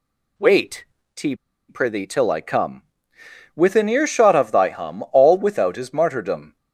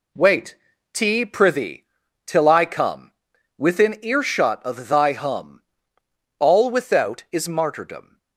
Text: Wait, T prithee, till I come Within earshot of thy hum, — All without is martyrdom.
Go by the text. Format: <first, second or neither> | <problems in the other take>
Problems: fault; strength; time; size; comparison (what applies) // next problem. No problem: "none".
second | pauses between "T" and "prithee"; slight; at 1.3 s; 0.34 s long // pauses between "come" and "Within"; noticeable; at 2.8 s; 0.74 s long; also in the second